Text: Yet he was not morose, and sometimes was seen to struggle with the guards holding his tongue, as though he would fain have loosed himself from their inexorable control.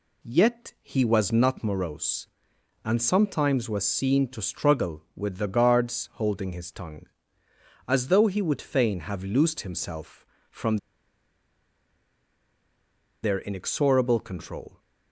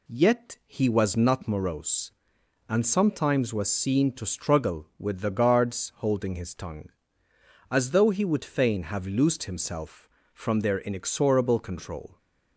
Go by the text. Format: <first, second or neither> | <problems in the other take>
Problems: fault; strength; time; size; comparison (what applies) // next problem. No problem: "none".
second | pauses between "from" and "their"; strong; at 10.7 s; 2.4 s long